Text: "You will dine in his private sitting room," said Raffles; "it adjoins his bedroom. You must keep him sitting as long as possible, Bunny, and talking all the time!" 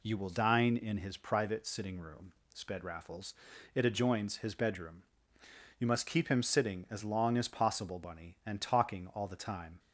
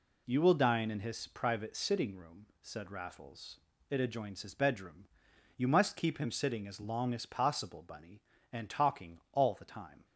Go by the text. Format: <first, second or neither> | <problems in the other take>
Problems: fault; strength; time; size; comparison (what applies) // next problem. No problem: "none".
second | says "sped" for "said"; at 2.5 s